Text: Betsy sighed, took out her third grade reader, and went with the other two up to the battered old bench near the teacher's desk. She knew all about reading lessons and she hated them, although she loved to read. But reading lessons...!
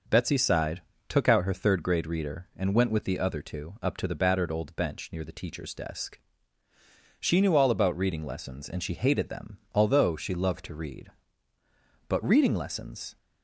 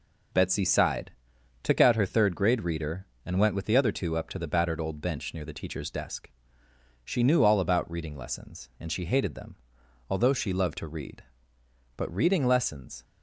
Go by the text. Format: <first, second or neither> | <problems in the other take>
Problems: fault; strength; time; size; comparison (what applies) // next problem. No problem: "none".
neither | none